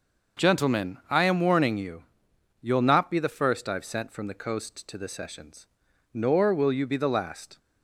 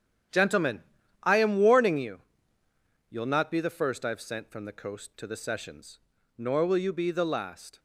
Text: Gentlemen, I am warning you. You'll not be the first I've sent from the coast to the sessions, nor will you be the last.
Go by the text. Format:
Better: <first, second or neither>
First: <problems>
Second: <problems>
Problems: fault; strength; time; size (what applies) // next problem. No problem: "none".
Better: first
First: starts louder than the rest; noticeable; until 1.5 s; 6 dB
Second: gets quieter; strong; throughout; 11.5 dB // starts louder than the rest; strong; until 1.7 s; 9 dB